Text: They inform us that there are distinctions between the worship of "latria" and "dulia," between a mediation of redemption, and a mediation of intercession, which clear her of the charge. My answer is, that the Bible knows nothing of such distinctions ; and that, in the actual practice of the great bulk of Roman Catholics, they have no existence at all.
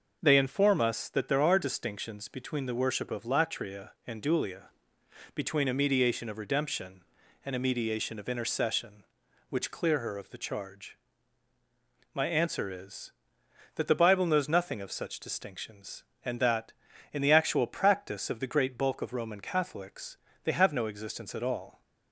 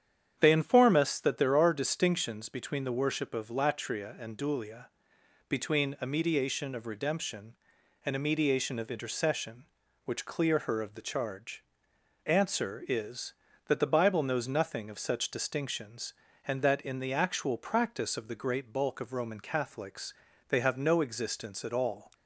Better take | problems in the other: first | starts louder than the rest; strong; until 1.4 s; 8.5 dB // skips "My"; at 11.9 s

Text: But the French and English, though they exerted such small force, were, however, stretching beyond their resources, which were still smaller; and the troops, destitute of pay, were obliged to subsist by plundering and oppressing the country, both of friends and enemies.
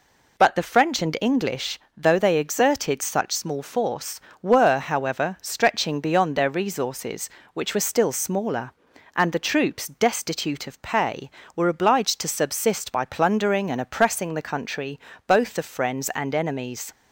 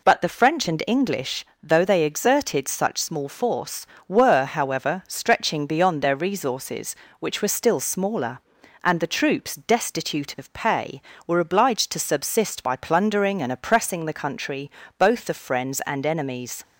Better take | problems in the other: neither | none

